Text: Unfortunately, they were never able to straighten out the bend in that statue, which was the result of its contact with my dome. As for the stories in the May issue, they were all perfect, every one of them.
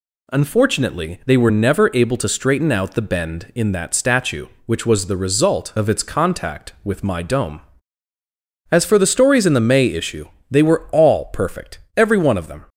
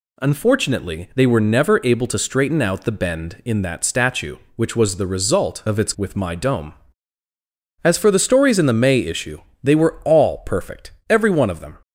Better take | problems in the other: first | skips "contact"; at 5.9 s

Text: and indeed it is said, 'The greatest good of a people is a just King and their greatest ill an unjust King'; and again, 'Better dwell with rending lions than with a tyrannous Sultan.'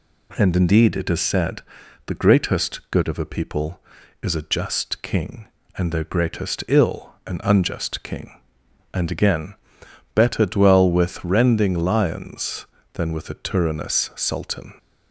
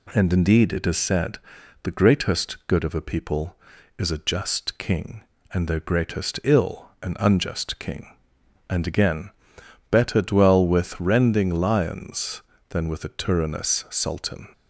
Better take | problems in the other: neither | none

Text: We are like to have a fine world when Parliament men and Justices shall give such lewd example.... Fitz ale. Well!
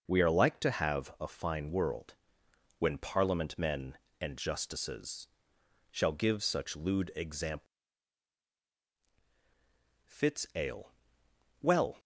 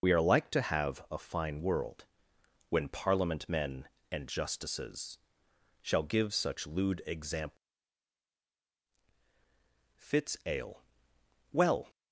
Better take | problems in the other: first | loses the start of "We"; at 0.0 s; 55 ms // pauses between "world" and "when"; noticeable; at 2.0 s; 0.64 s long; noticeable in the first // pauses between "Justices" and "shall"; noticeable; at 5.1 s; 0.64 s long; noticeable in the first

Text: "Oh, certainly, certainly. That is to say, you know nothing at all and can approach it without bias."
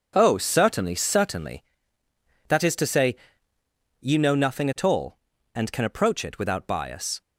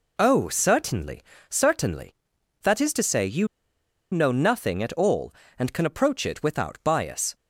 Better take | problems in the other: first | pauses between "you" and "know"; noticeable; at 3.4 s; 0.65 s long

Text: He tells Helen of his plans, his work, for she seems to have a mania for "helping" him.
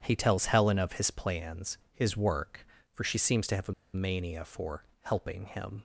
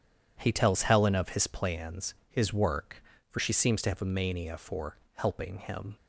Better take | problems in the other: second | pauses between "a" and "mania"; slight; at 3.7 s; 0.22 s long // pauses between "for" and "helping"; slight; at 4.8 s; 0.18 s long; slight in the second

